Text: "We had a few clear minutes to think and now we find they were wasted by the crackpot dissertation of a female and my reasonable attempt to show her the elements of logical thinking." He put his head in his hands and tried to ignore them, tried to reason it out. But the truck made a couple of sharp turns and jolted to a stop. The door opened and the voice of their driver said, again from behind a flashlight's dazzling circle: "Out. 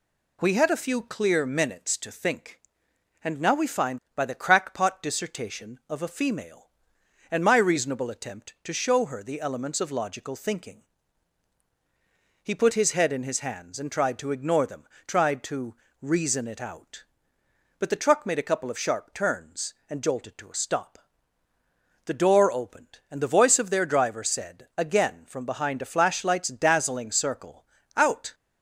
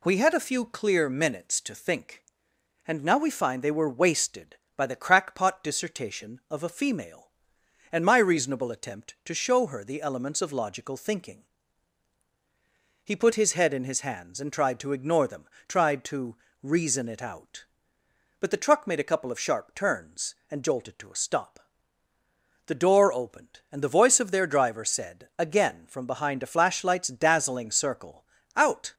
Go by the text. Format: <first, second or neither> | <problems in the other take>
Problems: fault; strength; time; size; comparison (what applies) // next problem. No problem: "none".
second | skips "they were wasted"; at 4.0 s // pauses between "to" and "reason"; slight; at 15.7 s; 0.26 s long; slight in the second